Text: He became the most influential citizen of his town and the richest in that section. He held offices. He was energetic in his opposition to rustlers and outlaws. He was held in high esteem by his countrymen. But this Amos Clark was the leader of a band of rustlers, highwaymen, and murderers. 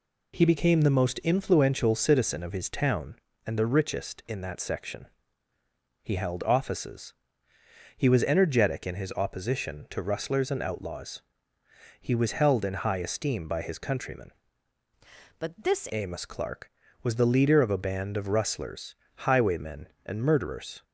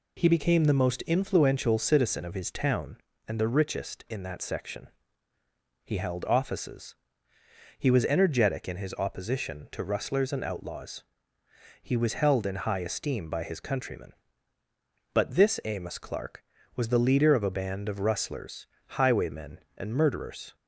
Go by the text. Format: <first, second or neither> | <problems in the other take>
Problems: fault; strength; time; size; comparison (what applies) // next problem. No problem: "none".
second | changes voice from "But" to "this"; from 15.3 to 15.8 s; 0.5 s long